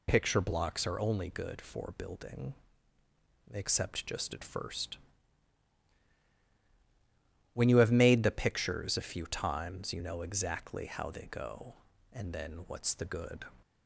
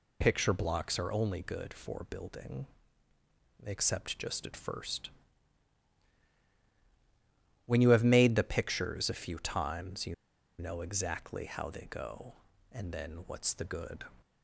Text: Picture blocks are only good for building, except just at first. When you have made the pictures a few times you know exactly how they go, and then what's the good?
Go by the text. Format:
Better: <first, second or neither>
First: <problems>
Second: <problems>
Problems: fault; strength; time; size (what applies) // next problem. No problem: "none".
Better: first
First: none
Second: pauses between "you" and "know"; at 10.1 s; 0.45 s long